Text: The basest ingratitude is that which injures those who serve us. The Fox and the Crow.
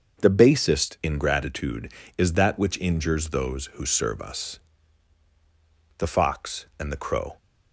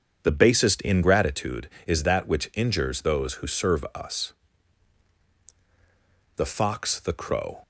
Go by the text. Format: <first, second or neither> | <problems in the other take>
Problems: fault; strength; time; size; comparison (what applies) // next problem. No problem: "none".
first | starts louder than the rest; strong; until 1.2 s; 7 dB // skips "and"; at 6.9 s